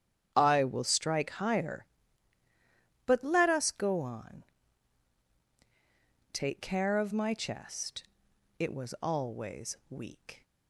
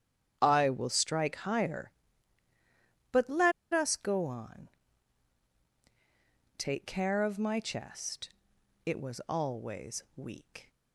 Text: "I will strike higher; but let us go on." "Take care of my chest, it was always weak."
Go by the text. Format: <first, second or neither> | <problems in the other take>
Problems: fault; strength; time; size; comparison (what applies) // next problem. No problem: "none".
first | starts louder than the rest; strong; until 1.4 s; 9 dB; strong in the first // pauses between "let" and "us"; slight; at 3.5 s; 0.21 s long